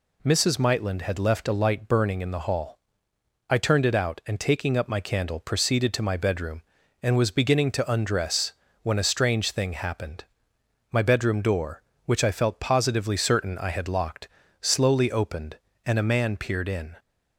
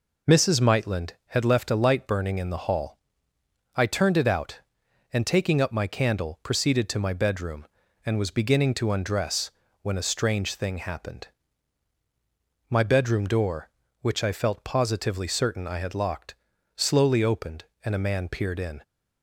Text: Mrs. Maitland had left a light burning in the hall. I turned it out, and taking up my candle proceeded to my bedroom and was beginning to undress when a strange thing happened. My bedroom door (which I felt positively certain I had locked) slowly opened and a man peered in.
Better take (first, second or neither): neither